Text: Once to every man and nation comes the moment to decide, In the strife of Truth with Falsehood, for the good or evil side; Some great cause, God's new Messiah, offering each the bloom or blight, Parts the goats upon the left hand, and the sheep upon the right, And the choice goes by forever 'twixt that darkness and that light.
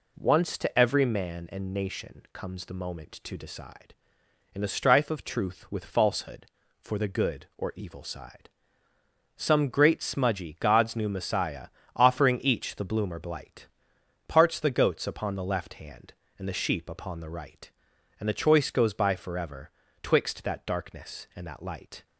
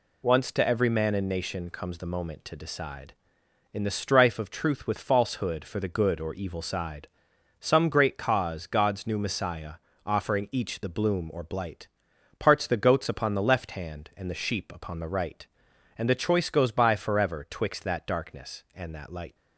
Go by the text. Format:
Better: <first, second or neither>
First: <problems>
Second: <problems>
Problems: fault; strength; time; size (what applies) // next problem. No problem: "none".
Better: second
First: says "smudgy" for "cause"; at 10.0 s // pauses between "forever" and "twixt"; slight; at 19.6 s; 0.32 s long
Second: none